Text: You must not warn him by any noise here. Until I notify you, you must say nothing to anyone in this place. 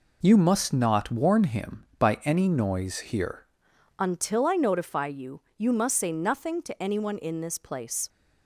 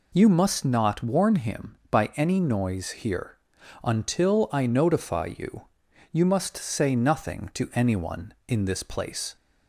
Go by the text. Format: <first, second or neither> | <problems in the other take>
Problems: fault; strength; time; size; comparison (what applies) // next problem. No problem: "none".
second | changes voice at "Until"; from 3.9 s on; 4.1 s long